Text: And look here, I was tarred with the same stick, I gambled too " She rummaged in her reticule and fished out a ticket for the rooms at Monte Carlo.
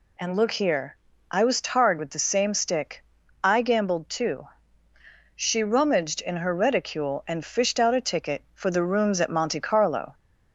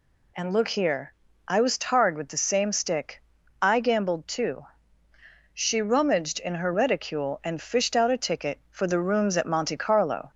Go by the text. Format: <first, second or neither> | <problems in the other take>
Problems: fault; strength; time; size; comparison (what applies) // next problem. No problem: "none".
neither | none